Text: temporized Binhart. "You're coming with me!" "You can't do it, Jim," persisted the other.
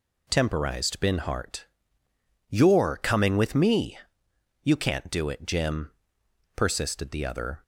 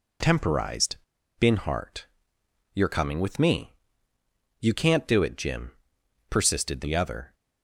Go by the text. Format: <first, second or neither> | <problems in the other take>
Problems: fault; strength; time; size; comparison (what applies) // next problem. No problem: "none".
first | pauses between "temporized" and "Binhart"; at 0.9 s; 0.42 s long